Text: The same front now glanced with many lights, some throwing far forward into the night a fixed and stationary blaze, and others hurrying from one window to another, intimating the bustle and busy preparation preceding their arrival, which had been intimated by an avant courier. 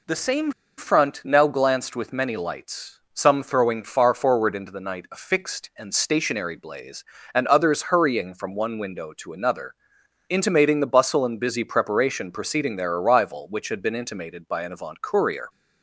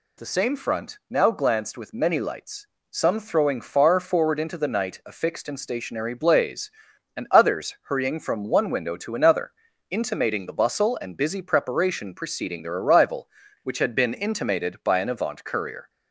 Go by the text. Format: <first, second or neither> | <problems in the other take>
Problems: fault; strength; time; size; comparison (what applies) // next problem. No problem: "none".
second | pauses between "same" and "front"; slight; at 0.5 s; 0.25 s long